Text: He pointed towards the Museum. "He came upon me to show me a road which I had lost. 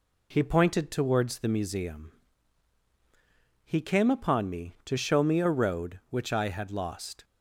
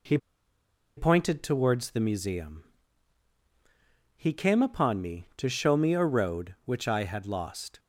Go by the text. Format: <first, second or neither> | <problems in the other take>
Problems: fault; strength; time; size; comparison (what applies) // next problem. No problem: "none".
first | pauses between "He" and "pointed"; noticeable; at 0.1 s; 0.78 s long